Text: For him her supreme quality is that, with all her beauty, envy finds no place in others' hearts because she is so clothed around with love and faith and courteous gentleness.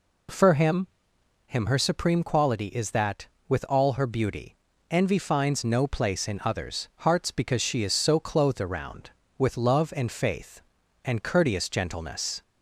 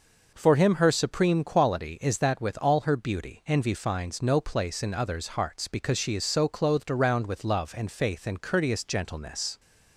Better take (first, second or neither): second